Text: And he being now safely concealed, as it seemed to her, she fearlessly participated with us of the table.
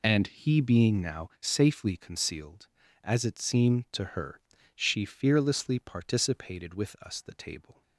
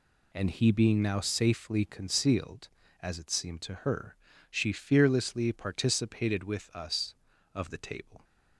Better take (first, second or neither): second